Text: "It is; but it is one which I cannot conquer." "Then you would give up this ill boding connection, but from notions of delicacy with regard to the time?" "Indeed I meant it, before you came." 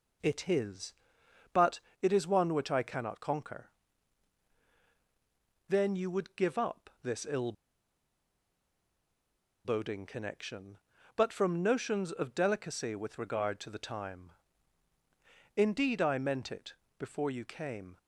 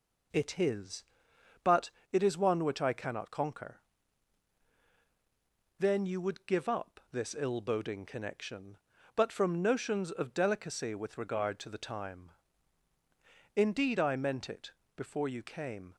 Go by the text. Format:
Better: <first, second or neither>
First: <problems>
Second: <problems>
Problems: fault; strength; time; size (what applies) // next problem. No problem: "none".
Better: second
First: pauses between "but" and "it"; slight; at 1.7 s; 0.22 s long // pauses between "ill" and "boding"; strong; at 7.5 s; 2.1 s long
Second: pauses between "but" and "it"; slight; at 1.9 s; 0.22 s long